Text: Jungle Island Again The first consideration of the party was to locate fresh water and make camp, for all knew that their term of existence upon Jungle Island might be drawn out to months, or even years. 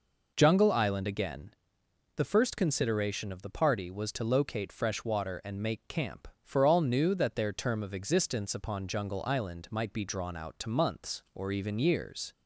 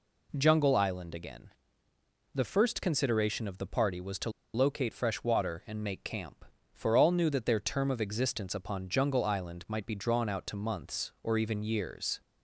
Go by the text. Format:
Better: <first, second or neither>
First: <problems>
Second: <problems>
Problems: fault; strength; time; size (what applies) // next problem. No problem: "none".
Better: first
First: pauses between "Again" and "The"; noticeable; at 1.5 s; 0.66 s long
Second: pauses between "Again" and "The"; noticeable; at 1.4 s; 0.84 s long // pauses between "to" and "locate"; slight; at 4.3 s; 0.23 s long